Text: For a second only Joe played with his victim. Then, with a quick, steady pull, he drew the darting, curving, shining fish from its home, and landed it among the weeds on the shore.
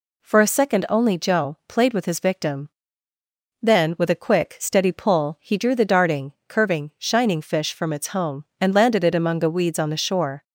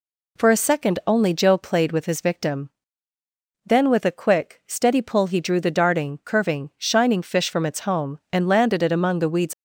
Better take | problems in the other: first | stops before "on the shore"; at 9.5 s

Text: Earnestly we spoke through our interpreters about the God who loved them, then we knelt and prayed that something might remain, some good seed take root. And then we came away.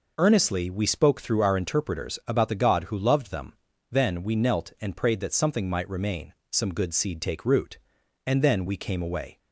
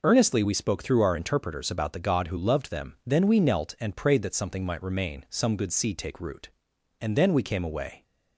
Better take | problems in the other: neither | none

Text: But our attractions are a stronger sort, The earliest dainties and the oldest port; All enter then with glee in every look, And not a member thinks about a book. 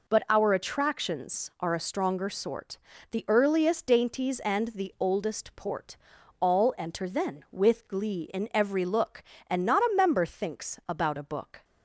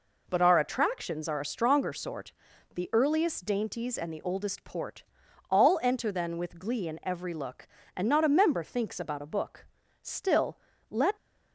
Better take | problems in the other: first | goes on to say "Still let"; noticeable; from 10.0 s on; 1.1 s long

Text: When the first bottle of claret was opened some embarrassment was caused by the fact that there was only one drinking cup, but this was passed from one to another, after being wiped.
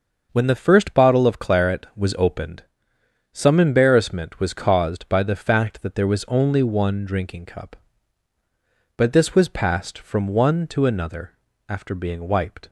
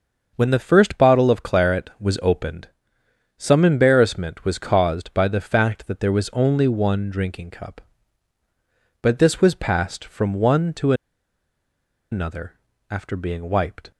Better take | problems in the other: first | starts louder than the rest; until 1.3 s; 6.5 dB; also in the first // pauses between "opened" and "some"; noticeable; at 2.6 s; 0.70 s long; noticeable in the first // pauses between "to" and "another"; at 10.9 s; 1.1 s long

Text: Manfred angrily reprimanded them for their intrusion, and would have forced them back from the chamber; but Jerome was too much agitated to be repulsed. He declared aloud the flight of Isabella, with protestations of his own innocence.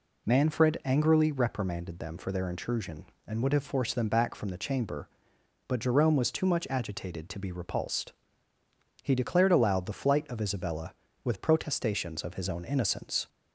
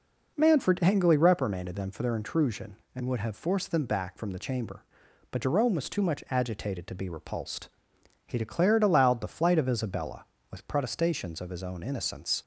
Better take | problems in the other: neither | none

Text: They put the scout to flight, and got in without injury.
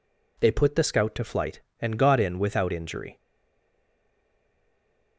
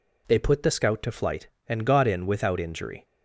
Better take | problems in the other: second | stays silent after the last word; noticeable; from 3.1 s on; 2.0 s long

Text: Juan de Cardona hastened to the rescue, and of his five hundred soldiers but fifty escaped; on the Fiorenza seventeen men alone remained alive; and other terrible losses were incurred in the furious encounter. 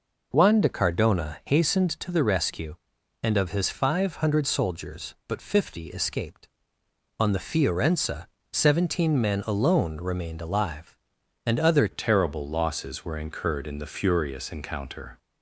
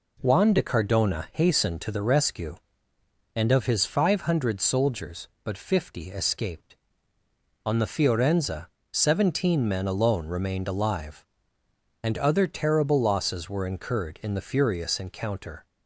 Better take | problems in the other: second | pauses between "Fiorenza" and "seventeen"; slight; at 8.2 s; 0.24 s long; slight in the second // changes voice at "terrible"; from 11.9 s on; 3.2 s long

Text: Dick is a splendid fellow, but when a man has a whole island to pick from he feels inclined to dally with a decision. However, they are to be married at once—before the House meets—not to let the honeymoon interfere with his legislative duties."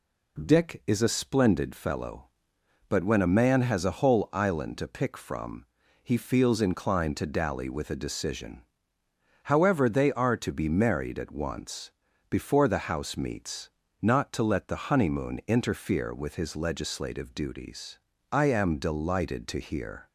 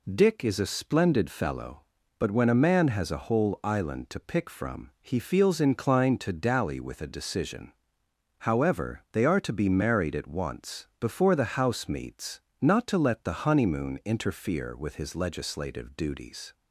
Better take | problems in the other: second | pauses between "from" and "he"; at 5.6 s; 0.38 s long // goes on to say "I am delighted to hear"; strong; from 18.3 s on; 1.7 s long

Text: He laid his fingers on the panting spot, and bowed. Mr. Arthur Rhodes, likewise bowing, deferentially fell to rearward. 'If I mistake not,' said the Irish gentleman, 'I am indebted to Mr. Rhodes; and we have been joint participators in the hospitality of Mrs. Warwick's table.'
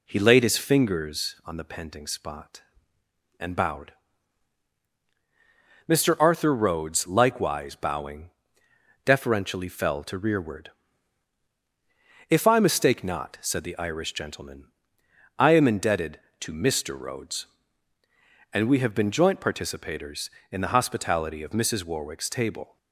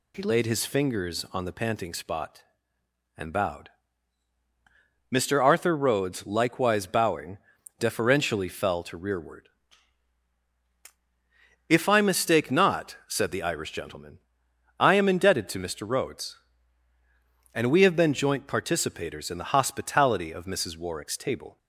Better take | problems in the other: neither | none

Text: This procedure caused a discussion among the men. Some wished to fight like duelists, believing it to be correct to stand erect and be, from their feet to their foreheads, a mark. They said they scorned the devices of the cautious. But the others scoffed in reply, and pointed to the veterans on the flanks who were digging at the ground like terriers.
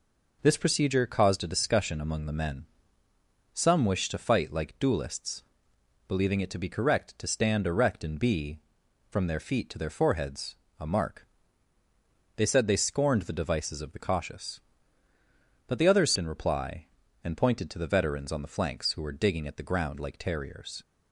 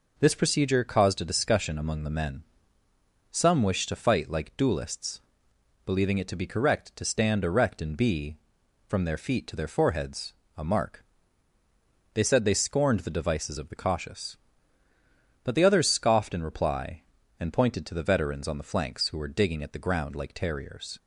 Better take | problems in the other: second | skips "scoffed"; at 16.1 s

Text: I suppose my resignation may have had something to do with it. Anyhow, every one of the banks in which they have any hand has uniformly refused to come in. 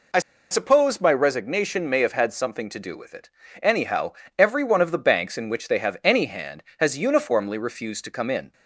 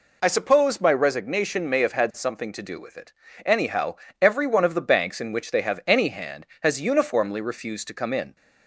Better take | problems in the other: second | pauses between "I" and "suppose"; slight; at 0.1 s; 0.31 s long

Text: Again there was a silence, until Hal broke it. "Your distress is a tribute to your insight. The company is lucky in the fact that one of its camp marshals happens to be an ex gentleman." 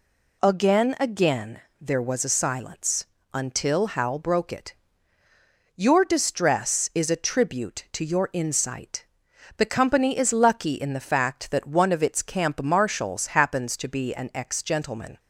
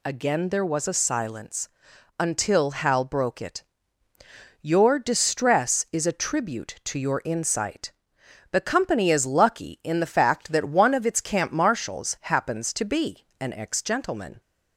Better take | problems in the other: second | says "Again" twice; at 1.0 s

